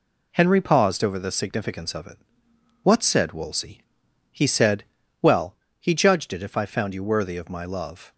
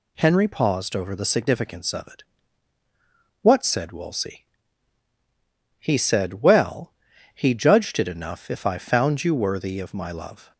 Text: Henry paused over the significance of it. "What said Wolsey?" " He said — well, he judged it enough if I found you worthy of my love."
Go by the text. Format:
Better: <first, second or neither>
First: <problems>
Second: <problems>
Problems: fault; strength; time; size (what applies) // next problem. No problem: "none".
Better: second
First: skips "enough"; at 6.4 s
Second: none